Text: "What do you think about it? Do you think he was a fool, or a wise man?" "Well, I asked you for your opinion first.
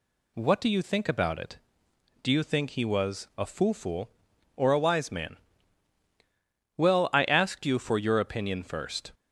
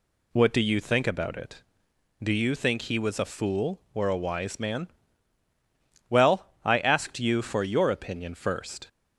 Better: second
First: says "fool" twice; at 3.7 s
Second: none

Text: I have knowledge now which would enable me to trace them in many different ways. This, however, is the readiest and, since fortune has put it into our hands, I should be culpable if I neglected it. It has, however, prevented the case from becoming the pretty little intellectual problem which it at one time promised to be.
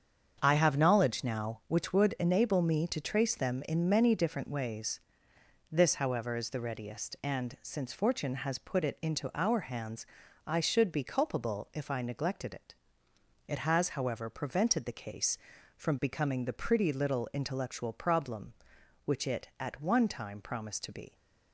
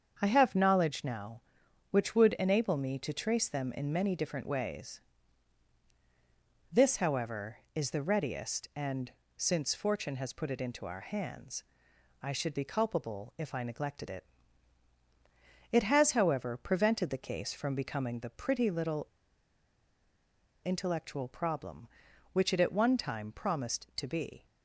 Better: first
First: starts louder than the rest; strong; until 1.4 s; 7.5 dB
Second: starts louder than the rest; until 1.2 s; 7 dB // pauses between "little" and "intellectual"; strong; at 19.0 s; 1.5 s long

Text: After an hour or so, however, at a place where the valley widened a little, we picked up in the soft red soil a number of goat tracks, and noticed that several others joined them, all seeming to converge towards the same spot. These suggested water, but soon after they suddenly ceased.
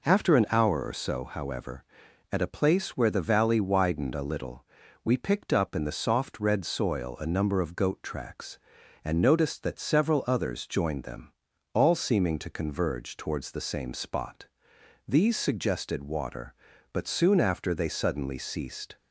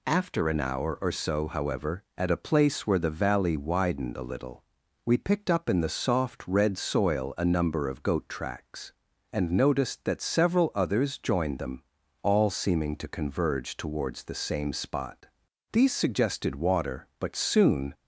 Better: first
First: none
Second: stops before "after they suddenly ceased"; at 17.9 s

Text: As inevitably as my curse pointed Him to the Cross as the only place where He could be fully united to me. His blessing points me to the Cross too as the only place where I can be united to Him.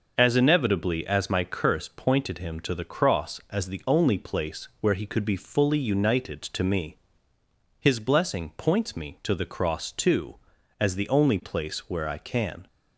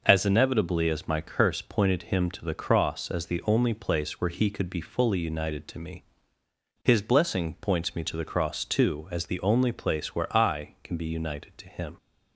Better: second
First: stops before "be united to Him"; at 12.6 s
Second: none

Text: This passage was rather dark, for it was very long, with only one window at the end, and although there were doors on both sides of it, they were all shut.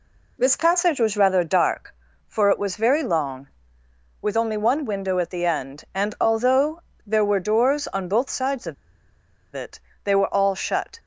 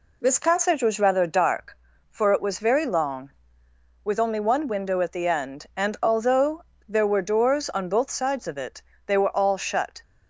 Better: second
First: pauses between "although" and "there"; slight; at 6.8 s; 0.24 s long // pauses between "of" and "it"; noticeable; at 8.7 s; 0.80 s long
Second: pauses between "although" and "there"; slight; at 6.6 s; 0.24 s long

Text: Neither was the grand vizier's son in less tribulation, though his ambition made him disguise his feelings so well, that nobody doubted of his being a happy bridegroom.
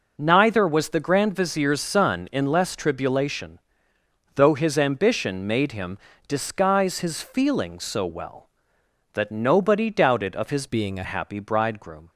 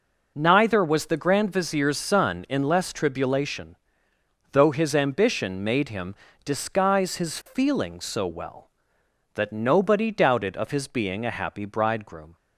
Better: second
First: pauses between "him" and "disguise"; slight; at 5.9 s; 0.32 s long // changes voice from "being" to "a"; from 10.6 to 11.0 s; 0.4 s long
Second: pauses between "him" and "disguise"; slight; at 6.1 s; 0.32 s long

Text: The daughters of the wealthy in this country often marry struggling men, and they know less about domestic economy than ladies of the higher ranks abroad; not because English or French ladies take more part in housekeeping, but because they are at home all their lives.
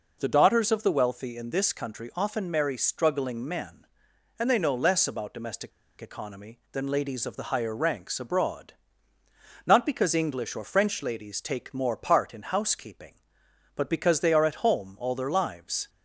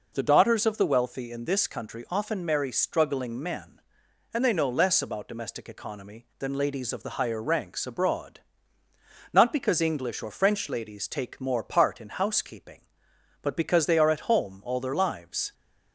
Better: second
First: pauses between "domestic" and "economy"; slight; at 5.7 s; 0.30 s long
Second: none

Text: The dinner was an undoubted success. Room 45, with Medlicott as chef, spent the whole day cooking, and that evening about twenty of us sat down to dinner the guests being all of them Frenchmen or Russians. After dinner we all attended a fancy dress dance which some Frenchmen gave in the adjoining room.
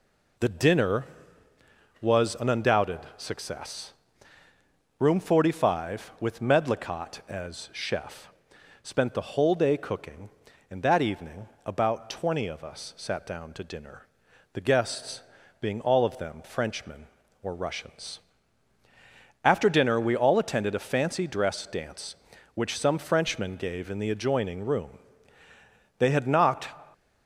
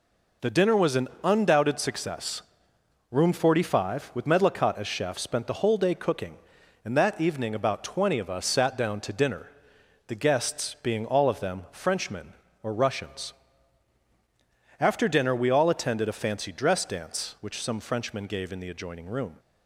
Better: second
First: pauses between "undoubted" and "success"; slight; at 2.9 s; 0.18 s long // pauses between "evening" and "about"; slight; at 11.4 s; 0.18 s long // pauses between "dinner" and "the"; noticeable; at 14.0 s; 0.52 s long // pauses between "guests" and "being"; at 15.2 s; 0.38 s long // goes on to say "They had knocked"; noticeable; from 25.9 s on; 0.78 s long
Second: pauses between "dinner" and "the"; noticeable; at 9.4 s; 0.60 s long

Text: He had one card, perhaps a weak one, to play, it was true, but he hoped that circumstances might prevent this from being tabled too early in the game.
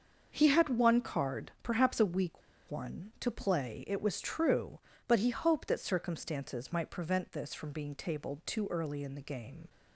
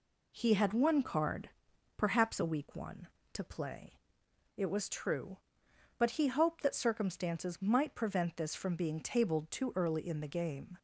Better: second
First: starts louder than the rest; until 1.3 s; 6.5 dB // pauses between "weak" and "one"; slight; at 2.4 s; 0.28 s long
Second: none

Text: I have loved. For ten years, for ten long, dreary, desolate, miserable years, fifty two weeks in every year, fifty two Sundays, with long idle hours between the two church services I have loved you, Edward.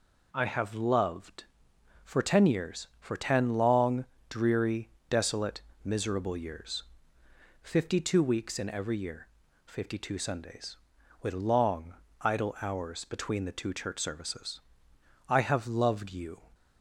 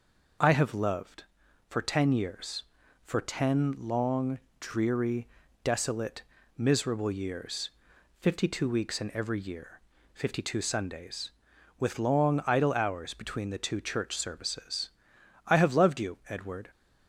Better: second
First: pauses between "long" and "idle"; slight; at 11.9 s; 0.26 s long // pauses between "services" and "I"; noticeable; at 14.6 s; 0.66 s long // stops before "Edward"; at 16.5 s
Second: pauses between "services" and "I"; noticeable; at 14.8 s; 0.58 s long

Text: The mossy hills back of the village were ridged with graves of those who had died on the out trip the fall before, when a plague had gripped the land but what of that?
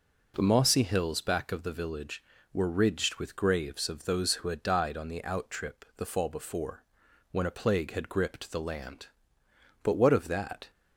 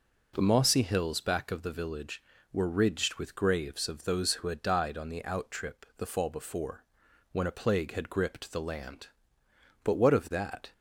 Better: neither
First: none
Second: none

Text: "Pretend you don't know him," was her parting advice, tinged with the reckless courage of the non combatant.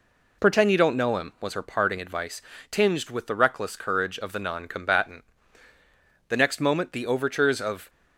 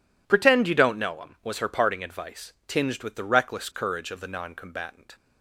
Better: second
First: goes on to say "The next moment the overtures of"; from 6.2 s on; 1.6 s long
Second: none

